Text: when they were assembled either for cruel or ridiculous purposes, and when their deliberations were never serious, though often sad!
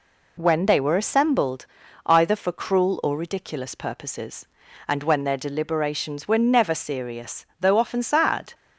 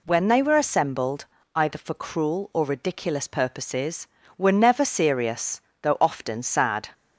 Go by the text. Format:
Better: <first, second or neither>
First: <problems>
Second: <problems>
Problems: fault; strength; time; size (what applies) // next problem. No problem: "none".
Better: first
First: pauses between "assembled" and "either"; at 1.6 s; 0.40 s long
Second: pauses between "assembled" and "either"; slight; at 1.2 s; 0.30 s long // skips "and when their deliberations"; at 4.2 s